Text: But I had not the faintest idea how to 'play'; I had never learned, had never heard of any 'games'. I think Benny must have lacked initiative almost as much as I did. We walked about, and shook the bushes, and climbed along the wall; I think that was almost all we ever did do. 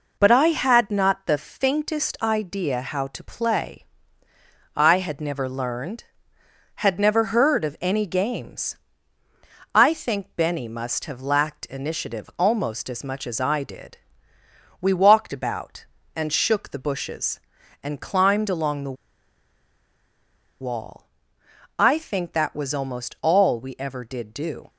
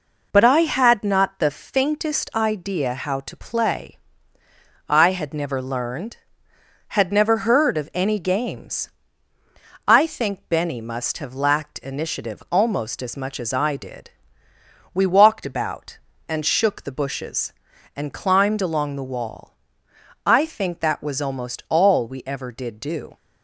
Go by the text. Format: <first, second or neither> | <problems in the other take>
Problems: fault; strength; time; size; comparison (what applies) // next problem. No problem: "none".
second | pauses between "the" and "wall"; strong; at 18.9 s; 1.6 s long